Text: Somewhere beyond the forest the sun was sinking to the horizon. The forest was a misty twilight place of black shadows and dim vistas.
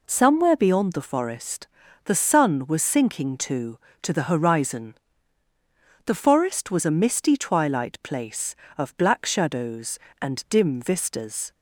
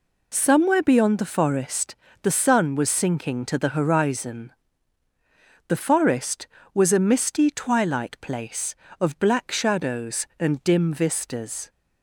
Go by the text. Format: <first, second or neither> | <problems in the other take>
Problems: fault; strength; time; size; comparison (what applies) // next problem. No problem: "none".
second | pauses between "forest" and "the"; at 1.6 s; 0.38 s long; slight in the second // says "to" twice; at 4.0 s